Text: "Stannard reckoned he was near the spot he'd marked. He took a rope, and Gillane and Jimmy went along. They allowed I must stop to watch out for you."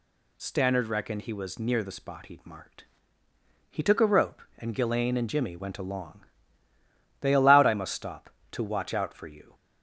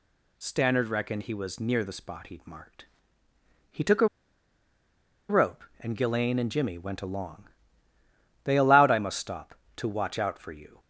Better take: first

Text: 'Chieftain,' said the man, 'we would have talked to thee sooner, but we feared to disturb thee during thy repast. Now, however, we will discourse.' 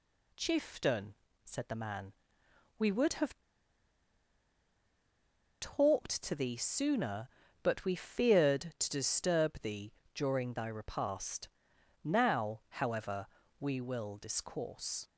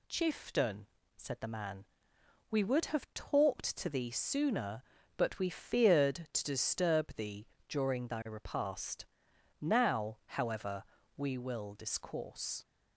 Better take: second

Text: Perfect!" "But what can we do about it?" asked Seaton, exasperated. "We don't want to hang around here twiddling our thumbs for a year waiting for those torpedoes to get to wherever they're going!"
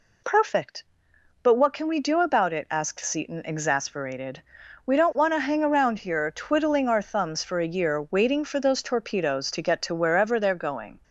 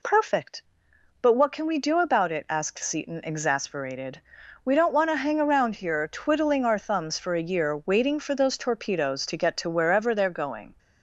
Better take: neither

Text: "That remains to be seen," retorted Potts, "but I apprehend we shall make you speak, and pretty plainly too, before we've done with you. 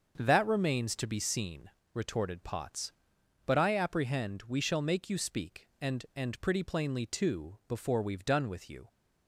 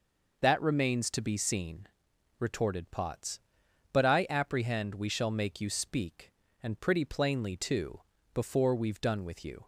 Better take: second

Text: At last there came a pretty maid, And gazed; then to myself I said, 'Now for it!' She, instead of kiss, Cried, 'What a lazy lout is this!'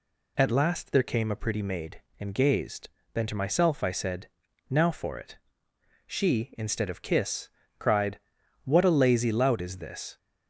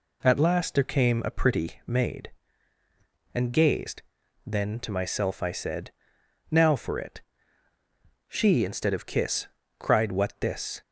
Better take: first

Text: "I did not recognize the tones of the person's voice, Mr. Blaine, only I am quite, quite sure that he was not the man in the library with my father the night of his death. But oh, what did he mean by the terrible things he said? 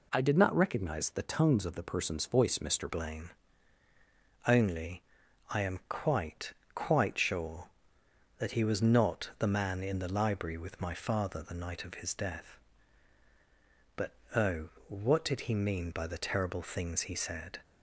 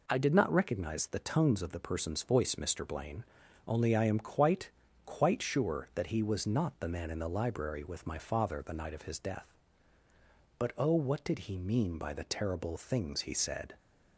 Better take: second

